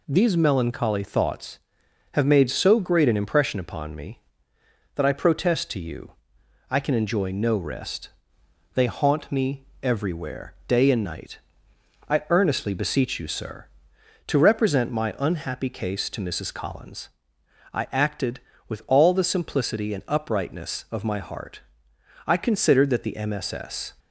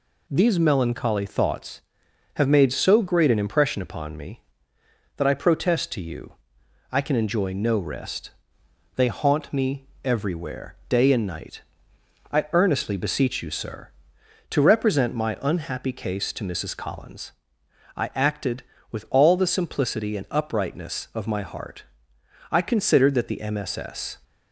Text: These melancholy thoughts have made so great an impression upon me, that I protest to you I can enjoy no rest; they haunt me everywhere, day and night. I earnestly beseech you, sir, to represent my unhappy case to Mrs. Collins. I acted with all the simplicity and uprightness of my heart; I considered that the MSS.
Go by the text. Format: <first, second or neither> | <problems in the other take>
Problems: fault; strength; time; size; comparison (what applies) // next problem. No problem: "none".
neither | pauses between "you" and "I"; noticeable; the same in both // pauses between "me" and "everywhere"; slight; the same in both